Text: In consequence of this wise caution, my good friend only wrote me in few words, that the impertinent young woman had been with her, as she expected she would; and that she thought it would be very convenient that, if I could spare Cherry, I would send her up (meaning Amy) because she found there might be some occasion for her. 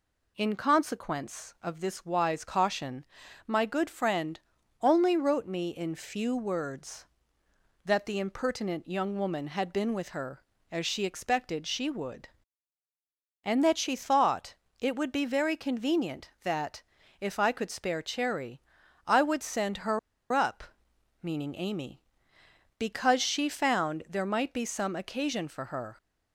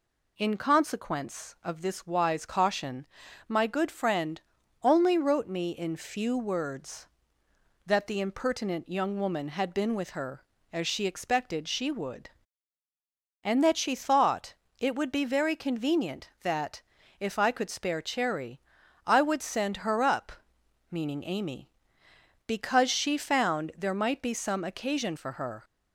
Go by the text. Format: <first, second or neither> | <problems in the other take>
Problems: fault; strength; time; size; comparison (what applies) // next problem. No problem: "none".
second | pauses between "friend" and "only"; at 4.4 s; 0.42 s long; also in the second // pauses between "thought" and "it"; slight; at 14.5 s; 0.24 s long; slight in the second // pauses between "her" and "up"; slight; at 19.9 s; 0.33 s long